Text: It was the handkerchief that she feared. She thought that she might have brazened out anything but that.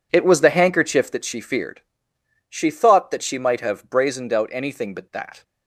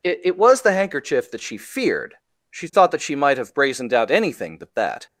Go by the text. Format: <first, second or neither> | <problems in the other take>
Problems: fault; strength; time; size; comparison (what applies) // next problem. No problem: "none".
first | says "It" twice; at 0.2 s